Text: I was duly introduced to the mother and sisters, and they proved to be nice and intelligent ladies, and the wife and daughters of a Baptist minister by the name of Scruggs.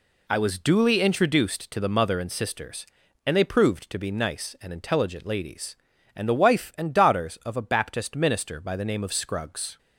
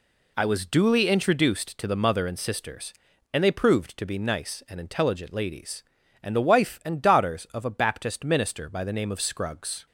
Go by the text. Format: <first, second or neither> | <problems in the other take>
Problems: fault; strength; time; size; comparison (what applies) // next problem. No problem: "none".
neither | none